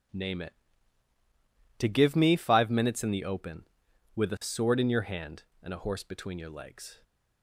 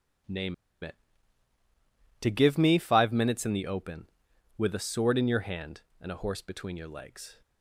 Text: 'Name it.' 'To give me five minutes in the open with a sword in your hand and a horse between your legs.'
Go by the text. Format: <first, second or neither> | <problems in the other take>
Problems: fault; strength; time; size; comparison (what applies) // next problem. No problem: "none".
first | pauses between "Name" and "it"; slight; at 0.5 s; 0.28 s long